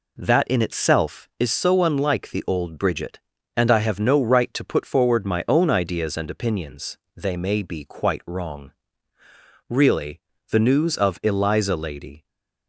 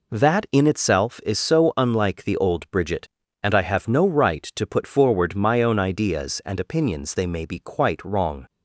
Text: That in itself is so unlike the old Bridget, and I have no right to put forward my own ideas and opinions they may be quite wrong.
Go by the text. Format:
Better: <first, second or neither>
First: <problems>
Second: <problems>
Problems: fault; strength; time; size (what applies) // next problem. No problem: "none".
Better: second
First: pauses between "opinions" and "they"; slight; at 6.9 s; 0.18 s long // goes on to say "Really the news of Eliza Lady"; strong; from 9.6 s on; 2.5 s long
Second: none